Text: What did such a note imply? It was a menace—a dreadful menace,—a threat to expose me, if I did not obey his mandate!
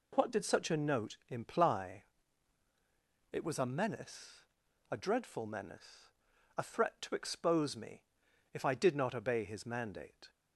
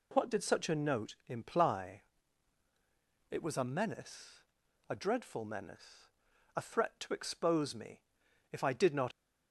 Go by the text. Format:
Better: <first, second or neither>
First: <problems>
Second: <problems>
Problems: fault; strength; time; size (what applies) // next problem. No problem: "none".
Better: first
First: none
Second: stops before "obey his mandate"; at 9.1 s